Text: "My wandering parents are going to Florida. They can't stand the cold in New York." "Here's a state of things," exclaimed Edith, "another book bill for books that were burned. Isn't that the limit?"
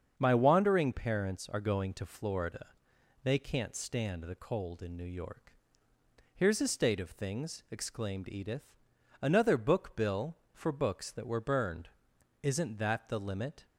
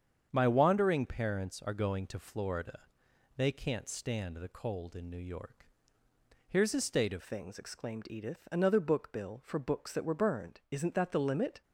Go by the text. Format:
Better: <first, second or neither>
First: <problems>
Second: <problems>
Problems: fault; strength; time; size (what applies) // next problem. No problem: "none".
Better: first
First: starts louder than the rest; until 1.1 s; 7 dB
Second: starts louder than the rest; strong; until 1.3 s; 7.5 dB // changes voice at "things"; from 7.2 s on; 4.4 s long